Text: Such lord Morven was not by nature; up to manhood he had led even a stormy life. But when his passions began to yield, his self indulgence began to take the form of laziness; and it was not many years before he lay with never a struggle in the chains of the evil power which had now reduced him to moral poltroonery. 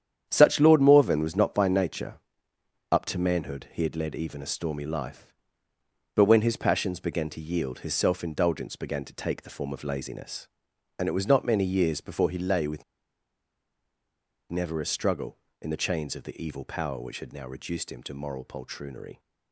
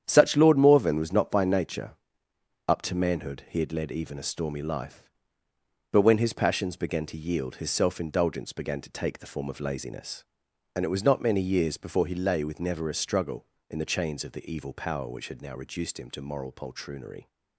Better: second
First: starts louder than the rest; strong; until 1.3 s; 9 dB // pauses between "with" and "never"; strong; at 12.8 s; 1.6 s long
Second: starts louder than the rest; strong; until 1.0 s; 9 dB

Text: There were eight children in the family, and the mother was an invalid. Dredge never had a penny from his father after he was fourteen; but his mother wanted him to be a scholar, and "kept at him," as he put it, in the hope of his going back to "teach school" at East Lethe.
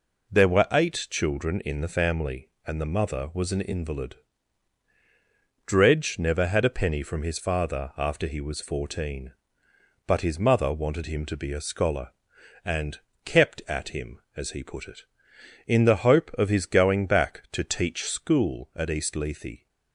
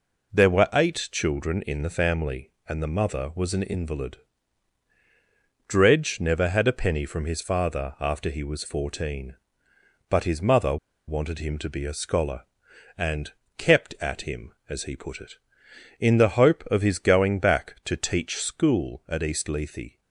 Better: first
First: pauses between "and" and "kept"; slight; at 12.9 s; 0.26 s long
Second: pauses between "mother" and "wanted"; slight; at 10.7 s; 0.31 s long // pauses between "and" and "kept"; slight; at 13.3 s; 0.26 s long

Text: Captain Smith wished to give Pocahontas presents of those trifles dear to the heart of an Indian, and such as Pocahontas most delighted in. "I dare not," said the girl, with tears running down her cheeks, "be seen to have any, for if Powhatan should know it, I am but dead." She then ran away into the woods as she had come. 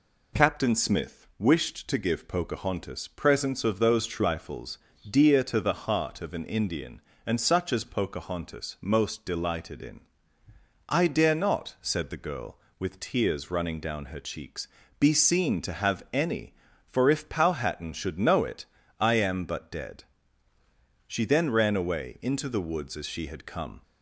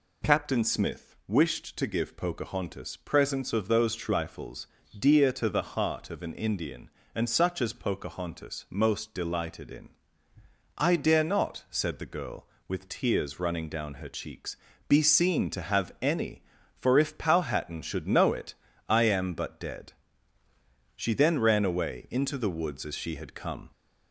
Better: first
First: pauses between "trifles" and "dear"; slight; at 4.7 s; 0.30 s long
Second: gets louder; slight; throughout; 2 dB // pauses between "trifles" and "dear"; slight; at 4.6 s; 0.30 s long

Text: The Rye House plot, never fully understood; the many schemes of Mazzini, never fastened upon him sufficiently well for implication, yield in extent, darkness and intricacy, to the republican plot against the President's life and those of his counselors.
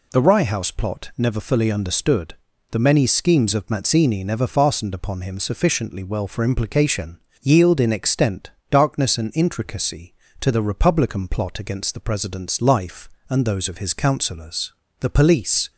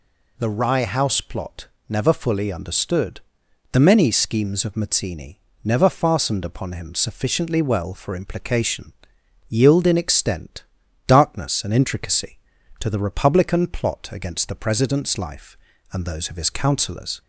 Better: second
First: goes on to say "The police"; noticeable; from 14.9 s on; 0.72 s long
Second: none

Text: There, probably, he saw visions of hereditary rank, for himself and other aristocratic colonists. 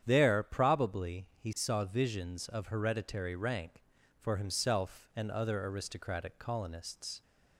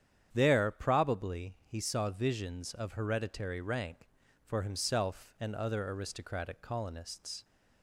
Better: neither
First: starts louder than the rest; strong; until 1.0 s; 9 dB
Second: starts louder than the rest; strong; until 1.3 s; 9 dB

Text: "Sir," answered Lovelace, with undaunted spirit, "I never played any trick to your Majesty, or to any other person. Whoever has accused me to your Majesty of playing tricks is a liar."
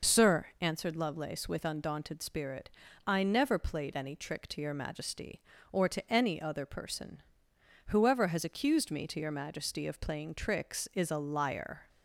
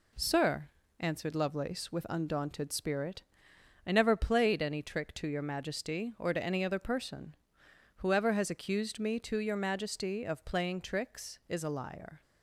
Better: second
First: loses the start of "Sir"; at 0.0 s; 50 ms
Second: none

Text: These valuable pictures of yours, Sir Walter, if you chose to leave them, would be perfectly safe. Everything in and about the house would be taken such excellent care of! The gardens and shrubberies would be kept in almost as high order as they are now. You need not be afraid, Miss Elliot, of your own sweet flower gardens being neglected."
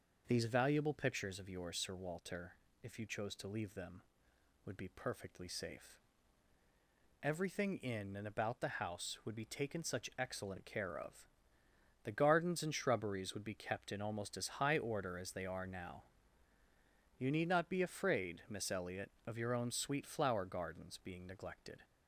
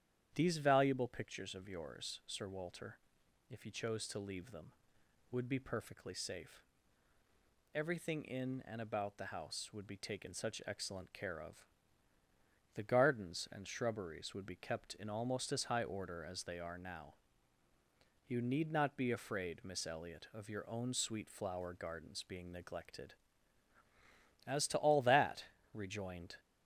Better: first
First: none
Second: starts louder than the rest; strong; until 1.3 s; 10 dB // goes on to say "As to all that rejoined"; strong; from 24.4 s on; 1.9 s long

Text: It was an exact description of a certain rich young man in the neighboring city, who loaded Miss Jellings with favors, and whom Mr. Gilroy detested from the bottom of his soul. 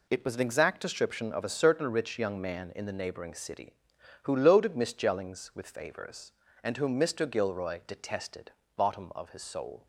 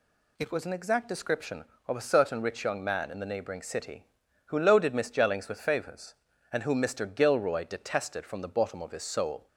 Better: second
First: skips "from the"; at 8.6 s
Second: none

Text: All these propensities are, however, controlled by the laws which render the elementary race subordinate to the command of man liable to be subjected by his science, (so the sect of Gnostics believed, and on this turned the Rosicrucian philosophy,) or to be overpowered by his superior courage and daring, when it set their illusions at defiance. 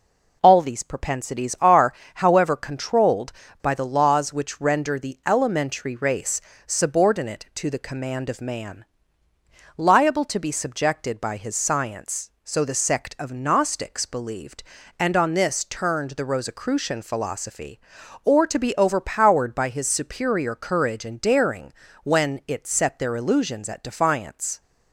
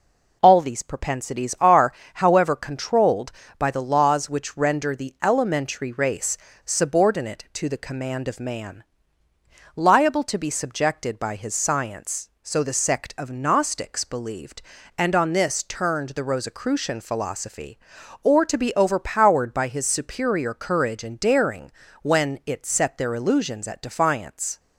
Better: neither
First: pauses between "race" and "subordinate"; slight; at 6.4 s; 0.26 s long // pauses between "man" and "liable"; noticeable; at 8.8 s; 0.94 s long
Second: pauses between "race" and "subordinate"; slight; at 6.3 s; 0.28 s long // pauses between "man" and "liable"; noticeable; at 8.8 s; 0.94 s long

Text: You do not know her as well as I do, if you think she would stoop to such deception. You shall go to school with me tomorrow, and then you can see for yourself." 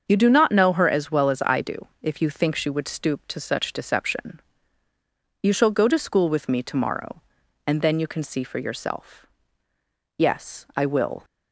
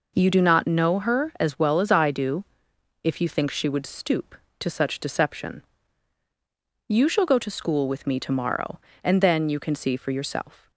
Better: second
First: starts louder than the rest; until 1.0 s; 7 dB // goes on to say "Yes I will"; noticeable; from 10.1 s on; 1.0 s long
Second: none

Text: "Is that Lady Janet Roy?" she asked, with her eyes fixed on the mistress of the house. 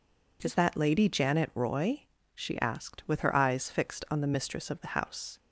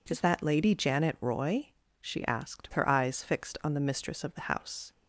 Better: first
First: none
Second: skips "with"; at 2.7 s

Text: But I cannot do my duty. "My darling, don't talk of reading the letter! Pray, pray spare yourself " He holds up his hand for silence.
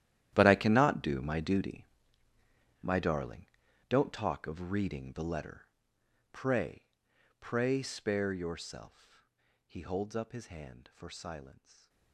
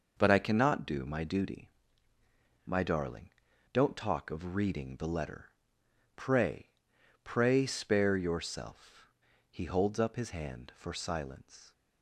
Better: second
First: gets quieter; strong; throughout; 19 dB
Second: none

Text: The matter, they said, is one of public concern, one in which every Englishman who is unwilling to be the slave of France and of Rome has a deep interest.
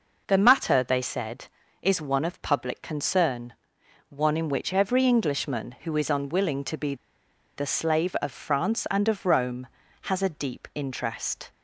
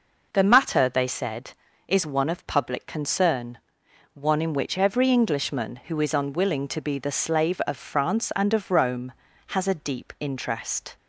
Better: second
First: pauses between "be" and "the"; noticeable; at 6.9 s; 0.61 s long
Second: none

